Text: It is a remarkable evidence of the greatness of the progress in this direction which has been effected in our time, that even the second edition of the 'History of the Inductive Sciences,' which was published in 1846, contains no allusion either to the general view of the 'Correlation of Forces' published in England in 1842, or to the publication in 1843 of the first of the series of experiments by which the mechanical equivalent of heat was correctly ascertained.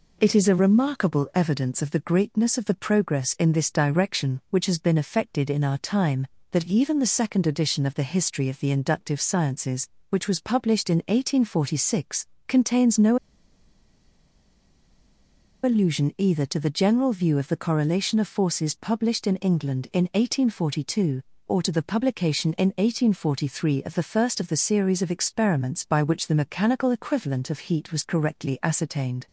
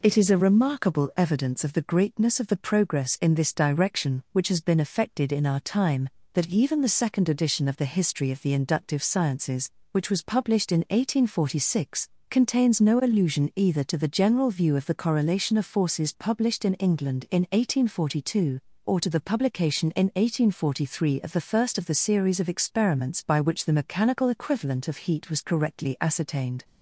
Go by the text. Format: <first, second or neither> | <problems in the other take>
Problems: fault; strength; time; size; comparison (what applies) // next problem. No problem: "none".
second | pauses between "no" and "allusion"; strong; at 13.1 s; 2.4 s long